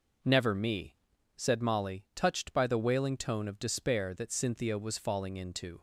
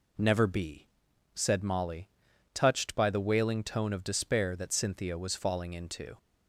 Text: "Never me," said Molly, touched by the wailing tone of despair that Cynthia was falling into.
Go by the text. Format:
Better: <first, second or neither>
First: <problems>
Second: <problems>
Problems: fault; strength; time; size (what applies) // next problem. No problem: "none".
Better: first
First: none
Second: says "be" for "me"; at 0.4 s